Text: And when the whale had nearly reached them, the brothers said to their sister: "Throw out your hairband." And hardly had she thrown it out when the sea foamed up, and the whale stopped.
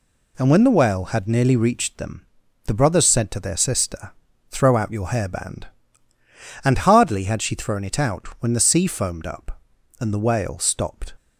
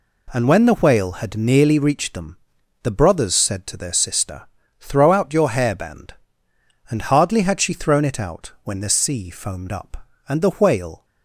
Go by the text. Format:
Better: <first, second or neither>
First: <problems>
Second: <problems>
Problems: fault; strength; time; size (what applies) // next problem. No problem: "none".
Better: first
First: none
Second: stops before "stopped"; at 11.0 s